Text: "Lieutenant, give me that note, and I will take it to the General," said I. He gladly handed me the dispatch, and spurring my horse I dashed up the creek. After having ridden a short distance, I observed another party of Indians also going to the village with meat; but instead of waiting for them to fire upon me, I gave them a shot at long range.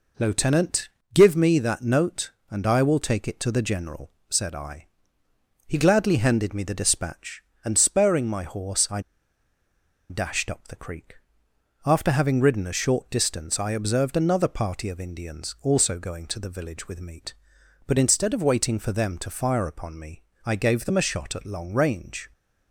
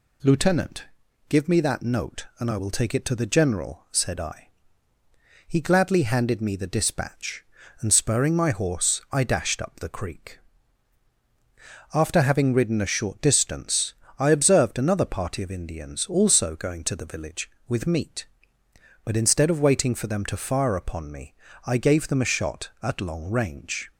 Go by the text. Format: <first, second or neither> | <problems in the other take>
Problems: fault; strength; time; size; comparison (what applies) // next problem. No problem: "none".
second | pauses between "I" and "dashed"; at 9.0 s; 1.0 s long